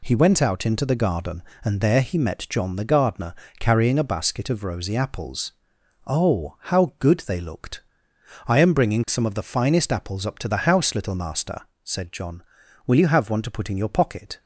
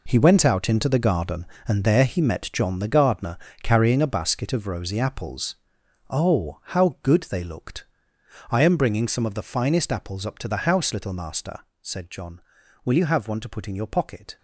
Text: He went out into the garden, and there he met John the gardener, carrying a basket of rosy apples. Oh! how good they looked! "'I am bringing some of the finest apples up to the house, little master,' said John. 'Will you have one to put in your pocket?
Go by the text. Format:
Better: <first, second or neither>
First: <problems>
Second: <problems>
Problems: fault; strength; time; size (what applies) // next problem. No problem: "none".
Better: first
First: none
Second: gets quieter; strong; throughout; 11 dB